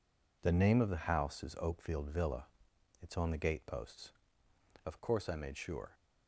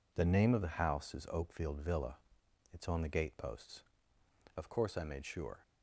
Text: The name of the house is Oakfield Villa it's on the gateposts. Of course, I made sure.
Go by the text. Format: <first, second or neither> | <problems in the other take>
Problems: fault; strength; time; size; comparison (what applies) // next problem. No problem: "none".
neither | pauses between "Villa" and "it's"; noticeable; the same in both